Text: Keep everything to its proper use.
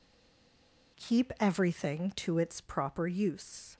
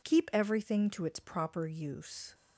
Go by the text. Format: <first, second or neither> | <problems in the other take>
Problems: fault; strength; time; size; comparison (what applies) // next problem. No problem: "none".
second | stays silent before the first word; until 0.9 s; 0.9 s long